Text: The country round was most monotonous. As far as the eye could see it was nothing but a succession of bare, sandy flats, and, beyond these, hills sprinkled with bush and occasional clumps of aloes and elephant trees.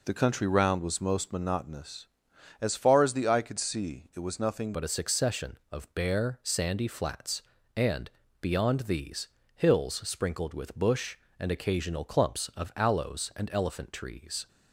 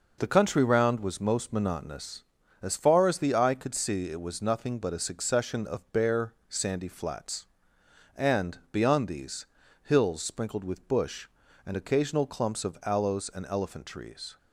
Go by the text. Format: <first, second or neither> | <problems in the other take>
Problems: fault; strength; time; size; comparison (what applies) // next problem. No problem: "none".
second | changes voice at "but"; from 4.7 s on; 9.7 s long